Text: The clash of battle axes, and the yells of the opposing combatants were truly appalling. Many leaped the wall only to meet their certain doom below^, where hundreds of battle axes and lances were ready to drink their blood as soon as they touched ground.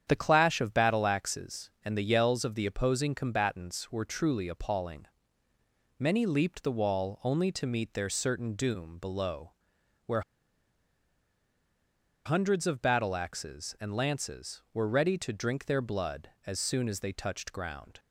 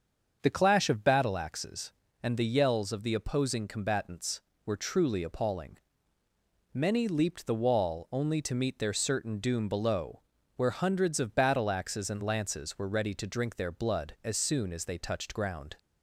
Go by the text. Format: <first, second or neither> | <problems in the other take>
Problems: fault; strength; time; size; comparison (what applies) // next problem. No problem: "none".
second | starts louder than the rest; strong; until 1.0 s; 8.5 dB; also in the second // pauses between "where" and "hundreds"; strong; at 10.2 s; 2.0 s long